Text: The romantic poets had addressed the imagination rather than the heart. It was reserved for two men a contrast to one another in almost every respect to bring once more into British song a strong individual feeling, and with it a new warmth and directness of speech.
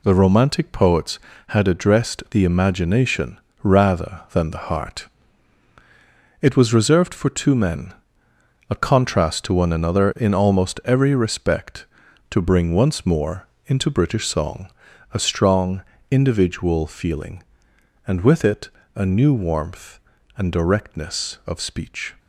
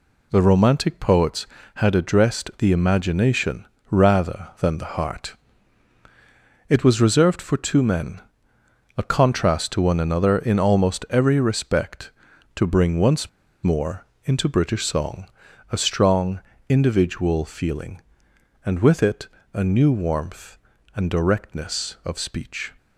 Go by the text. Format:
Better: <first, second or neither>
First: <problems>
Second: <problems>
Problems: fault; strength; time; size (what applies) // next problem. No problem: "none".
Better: first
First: pauses between "imagination" and "rather"; slight; at 3.3 s; 0.24 s long // pauses between "men" and "a"; noticeable; at 7.9 s; 0.76 s long // pauses between "more" and "into"; slight; at 13.4 s; 0.20 s long // pauses between "song" and "a"; noticeable; at 14.6 s; 0.48 s long // pauses between "strong" and "individual"; slight; at 15.8 s; 0.30 s long // pauses between "it" and "a"; slight; at 18.6 s; 0.26 s long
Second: pauses between "imagination" and "rather"; slight; at 3.6 s; 0.24 s long // pauses between "men" and "a"; noticeable; at 8.1 s; 0.76 s long // pauses between "once" and "more"; slight; at 13.2 s; 0.35 s long // pauses between "more" and "into"; slight; at 14.0 s; 0.20 s long // pauses between "song" and "a"; noticeable; at 15.2 s; 0.48 s long // pauses between "strong" and "individual"; slight; at 16.3 s; 0.30 s long // pauses between "it" and "a"; slight; at 19.2 s; 0.26 s long